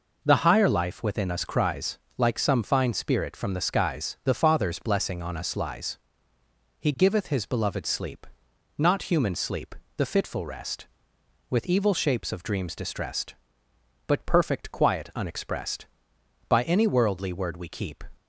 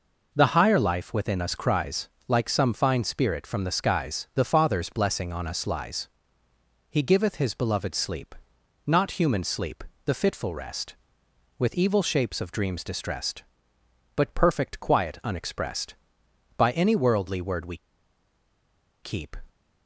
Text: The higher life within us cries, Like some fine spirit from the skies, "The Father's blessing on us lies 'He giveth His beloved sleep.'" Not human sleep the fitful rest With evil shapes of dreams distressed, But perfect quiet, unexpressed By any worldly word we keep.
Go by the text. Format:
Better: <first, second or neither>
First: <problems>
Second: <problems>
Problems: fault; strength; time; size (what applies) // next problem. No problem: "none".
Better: first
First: pauses between "lies" and "He"; noticeable; at 5.9 s; 0.80 s long // pauses between "sleep" and "the"; slight; at 9.7 s; 0.22 s long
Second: pauses between "lies" and "He"; noticeable; at 6.0 s; 0.80 s long // pauses between "sleep" and "the"; slight; at 9.8 s; 0.22 s long // pauses between "we" and "keep"; strong; at 17.7 s; 1.2 s long